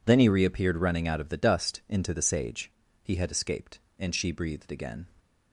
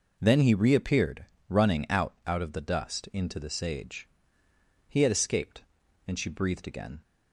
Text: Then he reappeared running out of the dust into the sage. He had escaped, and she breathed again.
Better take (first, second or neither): first